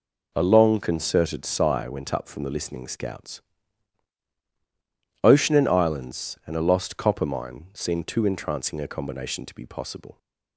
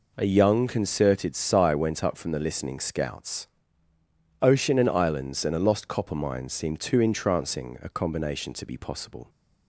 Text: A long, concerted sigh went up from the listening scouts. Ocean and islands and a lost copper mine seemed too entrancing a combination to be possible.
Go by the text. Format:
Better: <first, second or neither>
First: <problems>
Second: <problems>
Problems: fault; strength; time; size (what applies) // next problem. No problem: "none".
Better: first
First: none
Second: says "young" for "long"; at 0.2 s